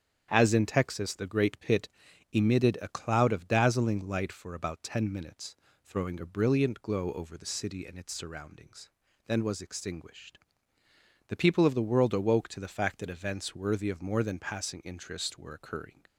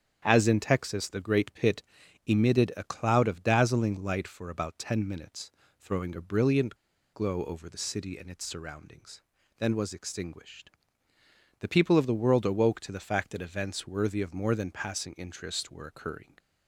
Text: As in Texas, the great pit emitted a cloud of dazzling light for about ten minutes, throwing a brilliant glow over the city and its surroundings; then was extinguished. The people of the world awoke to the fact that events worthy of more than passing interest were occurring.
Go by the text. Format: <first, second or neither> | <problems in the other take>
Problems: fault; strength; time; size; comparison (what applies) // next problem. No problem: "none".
first | starts louder than the rest; strong; until 1.2 s; 8.5 dB; strong in the first // pauses between "pit" and "emitted"; at 1.8 s; 0.42 s long; also in the first // pauses between "brilliant" and "glow"; at 6.7 s; 0.37 s long